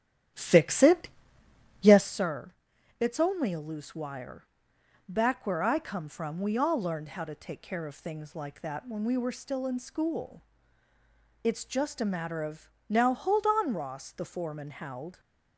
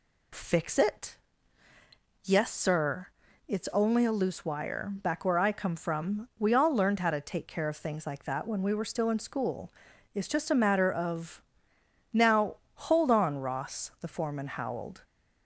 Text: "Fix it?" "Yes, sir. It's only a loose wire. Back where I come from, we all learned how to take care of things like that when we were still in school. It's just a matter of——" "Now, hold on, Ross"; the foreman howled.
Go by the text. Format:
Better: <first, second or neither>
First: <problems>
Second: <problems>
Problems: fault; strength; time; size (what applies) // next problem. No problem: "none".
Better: second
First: starts louder than the rest; strong; until 2.3 s; 10.5 dB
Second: none